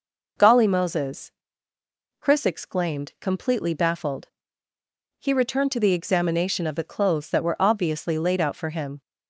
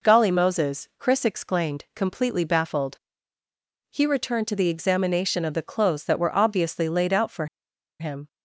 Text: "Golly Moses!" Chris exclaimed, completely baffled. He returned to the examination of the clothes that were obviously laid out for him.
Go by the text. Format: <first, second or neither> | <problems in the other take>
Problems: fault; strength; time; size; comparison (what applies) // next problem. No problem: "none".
first | pauses between "for" and "him"; noticeable; at 7.4 s; 0.52 s long